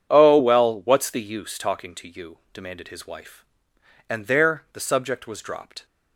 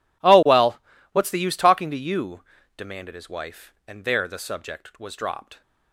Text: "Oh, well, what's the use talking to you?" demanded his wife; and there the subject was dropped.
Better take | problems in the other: neither | none

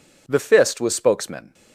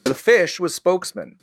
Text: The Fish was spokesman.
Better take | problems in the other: second | says "Fist" for "Fish"; at 0.3 s

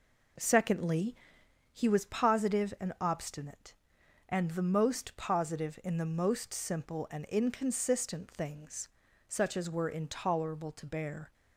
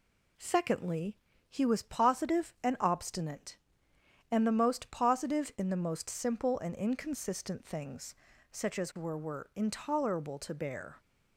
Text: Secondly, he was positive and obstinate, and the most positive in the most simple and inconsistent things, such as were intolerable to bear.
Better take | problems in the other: first | says "were" twice; at 9.1 s

